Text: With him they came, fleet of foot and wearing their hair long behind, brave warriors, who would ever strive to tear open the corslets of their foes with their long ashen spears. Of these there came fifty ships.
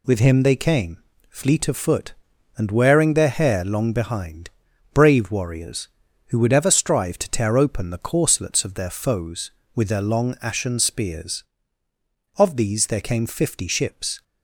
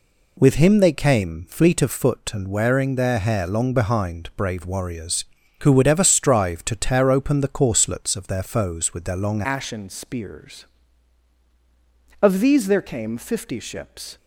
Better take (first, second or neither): first